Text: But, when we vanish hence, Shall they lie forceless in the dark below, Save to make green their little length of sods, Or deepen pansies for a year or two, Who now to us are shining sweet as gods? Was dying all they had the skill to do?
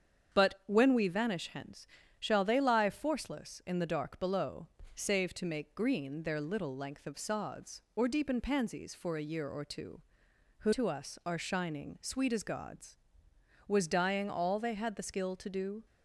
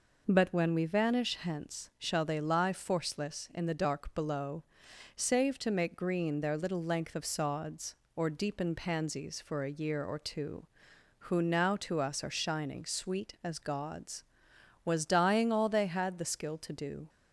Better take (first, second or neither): second